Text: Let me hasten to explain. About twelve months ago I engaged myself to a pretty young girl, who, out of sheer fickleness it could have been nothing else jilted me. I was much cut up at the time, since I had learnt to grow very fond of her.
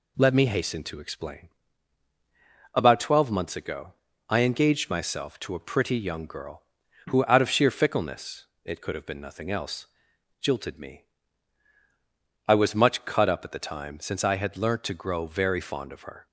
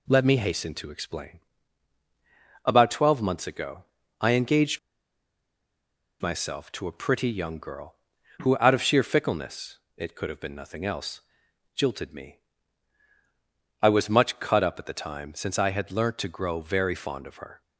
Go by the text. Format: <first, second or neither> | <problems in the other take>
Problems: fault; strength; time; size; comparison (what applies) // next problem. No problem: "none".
first | pauses between "ago" and "I"; slight; at 3.8 s; 0.34 s long; slight in the first // pauses between "engaged" and "myself"; strong; at 4.7 s; 1.4 s long // pauses between "fickleness" and "it"; slight; at 9.7 s; 0.18 s long; slight in the first // pauses between "else" and "jilted"; noticeable; at 11.2 s; 0.52 s long; noticeable in the first